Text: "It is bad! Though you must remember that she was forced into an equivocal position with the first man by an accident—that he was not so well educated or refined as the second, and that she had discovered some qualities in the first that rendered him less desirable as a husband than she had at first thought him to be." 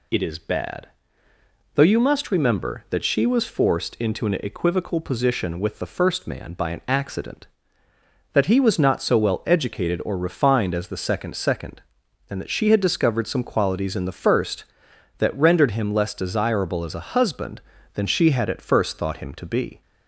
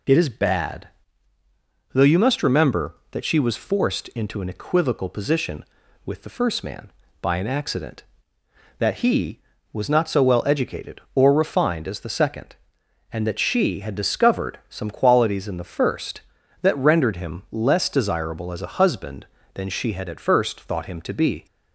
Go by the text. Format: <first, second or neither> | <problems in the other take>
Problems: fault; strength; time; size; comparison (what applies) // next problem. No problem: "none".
second | says "second" twice; at 11.3 s